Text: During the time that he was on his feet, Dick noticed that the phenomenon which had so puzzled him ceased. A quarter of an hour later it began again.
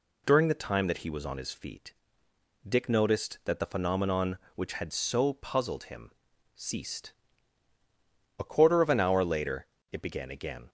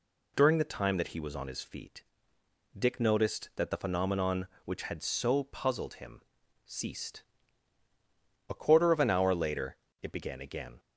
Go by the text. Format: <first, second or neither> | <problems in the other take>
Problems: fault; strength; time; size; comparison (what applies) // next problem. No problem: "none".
neither | pauses between "him" and "ceased"; the same in both // pauses between "later" and "it"; slight; the same in both